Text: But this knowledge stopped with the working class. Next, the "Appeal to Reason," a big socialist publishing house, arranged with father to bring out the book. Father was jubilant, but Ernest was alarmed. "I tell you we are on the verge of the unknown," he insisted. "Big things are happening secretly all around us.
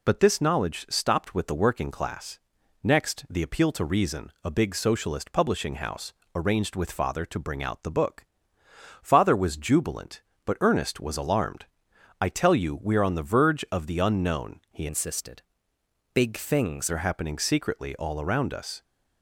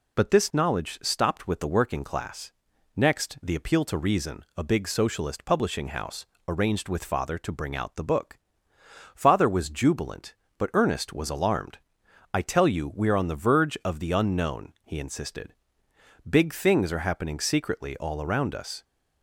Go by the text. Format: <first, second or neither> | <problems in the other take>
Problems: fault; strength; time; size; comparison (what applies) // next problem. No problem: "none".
second | changes voice from "insisted" to "things"; from 14.8 to 16.9 s; 2.1 s long